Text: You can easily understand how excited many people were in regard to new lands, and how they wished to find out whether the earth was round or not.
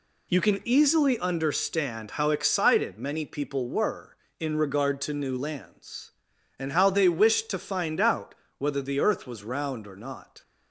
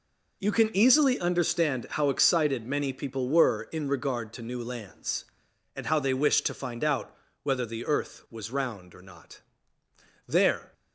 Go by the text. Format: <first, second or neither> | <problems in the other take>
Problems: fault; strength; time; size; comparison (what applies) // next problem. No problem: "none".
first | pauses between "out" and "whether"; slight; at 7.1 s; 0.30 s long; slight in the first // goes on to say "There"; slight; from 10.2 s on; 0.46 s long